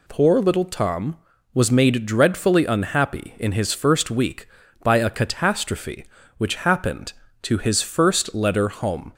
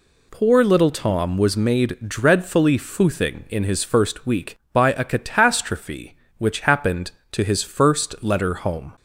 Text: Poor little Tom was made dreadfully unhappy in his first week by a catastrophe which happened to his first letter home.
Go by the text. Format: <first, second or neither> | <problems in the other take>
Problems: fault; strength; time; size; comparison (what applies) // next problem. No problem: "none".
first | says "foothing" for "unhappy"; at 2.7 s